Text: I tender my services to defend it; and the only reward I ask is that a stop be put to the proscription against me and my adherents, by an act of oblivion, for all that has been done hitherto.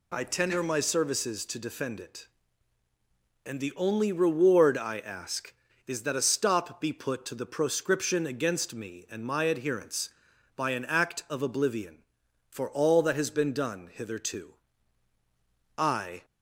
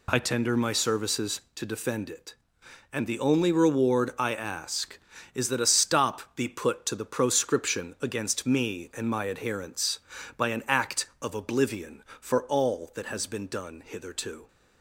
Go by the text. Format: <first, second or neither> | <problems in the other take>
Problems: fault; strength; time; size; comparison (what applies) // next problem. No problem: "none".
second | goes on to say "I"; slight; from 15.7 s on; 0.46 s long